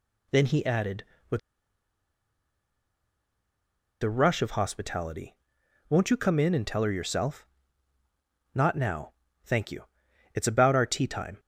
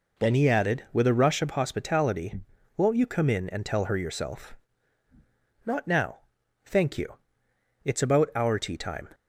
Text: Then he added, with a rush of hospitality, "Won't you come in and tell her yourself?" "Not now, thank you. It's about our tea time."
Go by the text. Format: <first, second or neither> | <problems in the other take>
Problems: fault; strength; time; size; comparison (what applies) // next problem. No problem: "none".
second | pauses between "with" and "a"; strong; at 1.3 s; 2.6 s long